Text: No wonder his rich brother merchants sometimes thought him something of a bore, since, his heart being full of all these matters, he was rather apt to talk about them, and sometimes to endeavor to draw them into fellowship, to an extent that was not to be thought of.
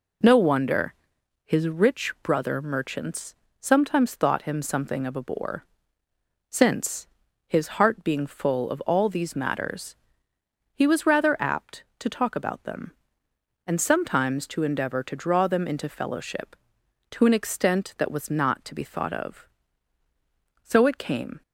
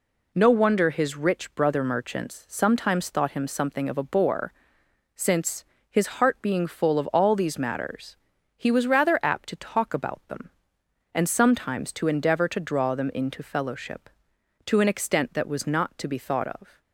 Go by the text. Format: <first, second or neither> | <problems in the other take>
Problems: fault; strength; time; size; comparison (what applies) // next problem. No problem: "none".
second | pauses between "wonder" and "his"; noticeable; at 0.9 s; 0.50 s long // pauses between "merchants" and "sometimes"; slight; at 3.3 s; 0.26 s long // goes on to say "So it came"; noticeable; from 20.6 s on; 0.80 s long